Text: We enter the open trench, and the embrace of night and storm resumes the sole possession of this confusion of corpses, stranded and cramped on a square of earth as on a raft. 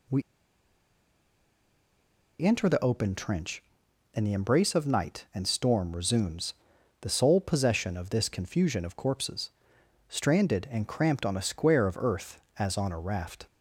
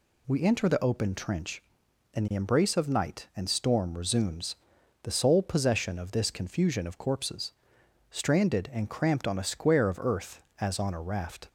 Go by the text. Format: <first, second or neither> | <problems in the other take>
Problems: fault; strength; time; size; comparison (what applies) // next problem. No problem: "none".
second | pauses between "We" and "enter"; strong; at 0.2 s; 2.1 s long // pauses between "resumes" and "the"; noticeable; at 6.5 s; 0.48 s long; noticeable in the second